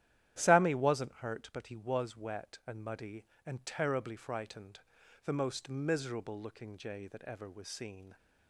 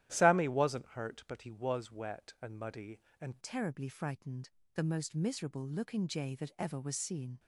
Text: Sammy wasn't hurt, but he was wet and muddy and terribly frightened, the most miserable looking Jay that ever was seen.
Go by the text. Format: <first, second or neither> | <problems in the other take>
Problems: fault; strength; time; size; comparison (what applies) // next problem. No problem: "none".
first | starts louder than the rest; strong; until 1.1 s; 12.5 dB; strong in the first // changes voice at "terribly"; from 3.4 s on; 3.9 s long